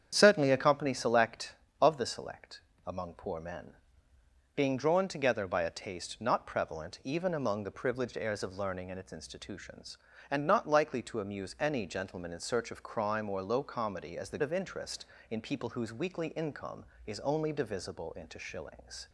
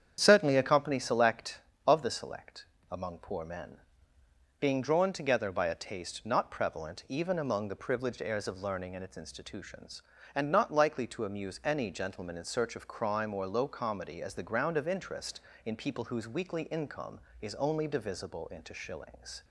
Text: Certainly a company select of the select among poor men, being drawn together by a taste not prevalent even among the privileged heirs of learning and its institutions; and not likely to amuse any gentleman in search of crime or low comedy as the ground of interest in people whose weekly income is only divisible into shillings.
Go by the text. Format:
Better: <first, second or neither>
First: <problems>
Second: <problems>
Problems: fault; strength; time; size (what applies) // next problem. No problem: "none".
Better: second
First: starts louder than the rest; strong; until 1.1 s; 8.5 dB // pauses between "select" and "among"; slight; at 2.6 s; 0.24 s long // skips "ground"; at 14.4 s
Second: starts louder than the rest; strong; until 1.2 s; 8.5 dB // pauses between "select" and "among"; slight; at 2.6 s; 0.24 s long